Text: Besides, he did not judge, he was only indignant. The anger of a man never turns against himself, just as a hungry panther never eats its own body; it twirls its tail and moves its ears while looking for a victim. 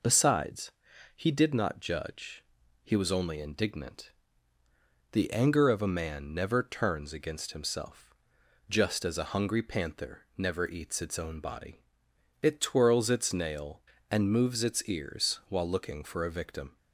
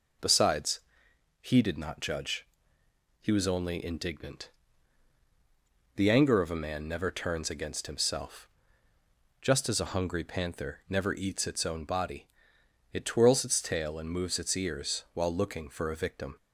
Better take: second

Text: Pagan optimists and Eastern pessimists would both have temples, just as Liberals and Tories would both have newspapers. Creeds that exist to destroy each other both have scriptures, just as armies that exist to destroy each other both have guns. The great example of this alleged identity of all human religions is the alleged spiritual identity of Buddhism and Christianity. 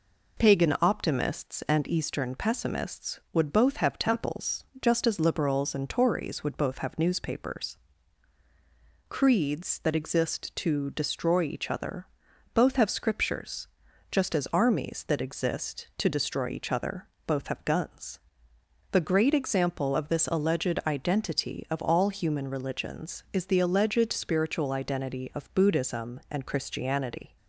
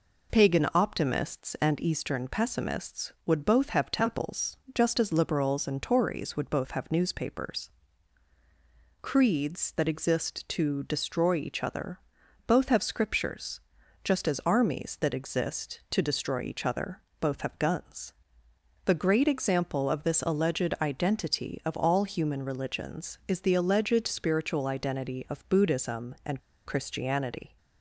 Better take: first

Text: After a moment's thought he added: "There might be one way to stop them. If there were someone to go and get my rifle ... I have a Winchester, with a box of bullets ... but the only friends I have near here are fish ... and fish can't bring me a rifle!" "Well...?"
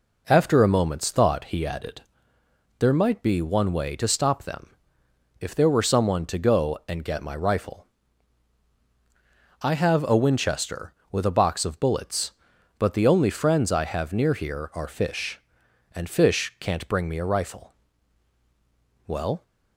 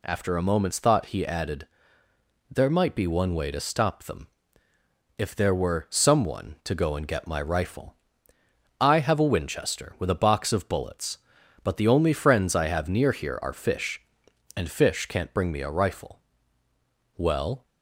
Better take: neither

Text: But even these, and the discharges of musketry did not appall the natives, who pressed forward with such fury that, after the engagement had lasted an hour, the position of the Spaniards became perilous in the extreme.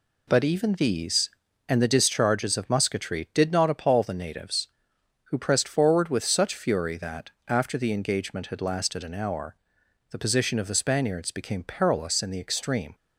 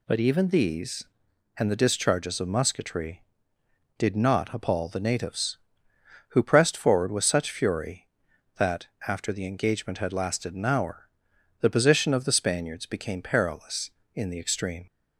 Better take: neither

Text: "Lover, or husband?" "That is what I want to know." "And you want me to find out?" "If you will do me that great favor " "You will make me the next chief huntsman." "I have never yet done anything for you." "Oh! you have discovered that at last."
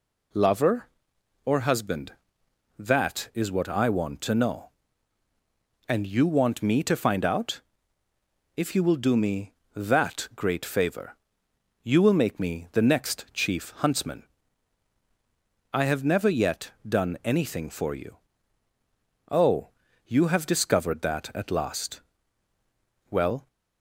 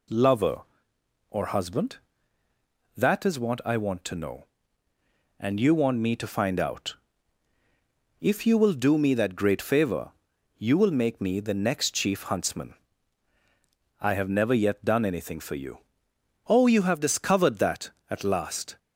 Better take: second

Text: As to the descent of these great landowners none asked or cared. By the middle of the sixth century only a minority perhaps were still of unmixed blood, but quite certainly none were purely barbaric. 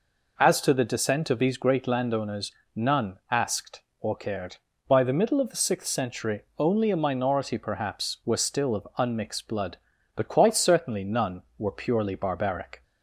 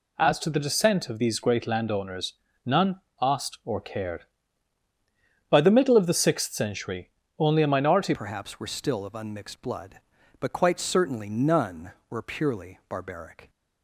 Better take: first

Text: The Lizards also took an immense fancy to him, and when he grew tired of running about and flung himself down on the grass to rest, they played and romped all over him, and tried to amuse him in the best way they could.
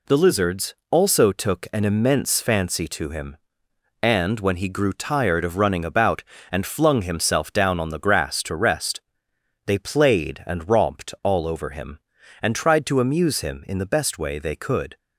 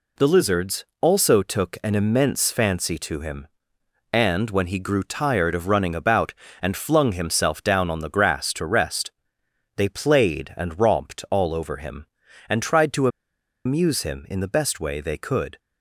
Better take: first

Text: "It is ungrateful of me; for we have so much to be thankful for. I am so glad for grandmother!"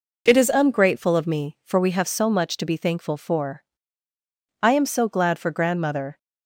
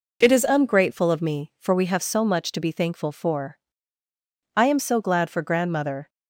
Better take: neither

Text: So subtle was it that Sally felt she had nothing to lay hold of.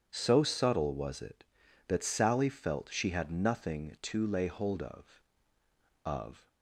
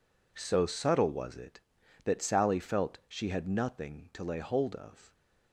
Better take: second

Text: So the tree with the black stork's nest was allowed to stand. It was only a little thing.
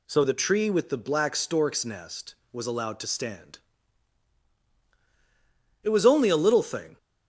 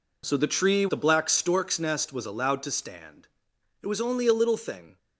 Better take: first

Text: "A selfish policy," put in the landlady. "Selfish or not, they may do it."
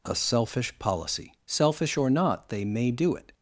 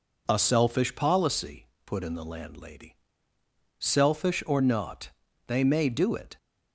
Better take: second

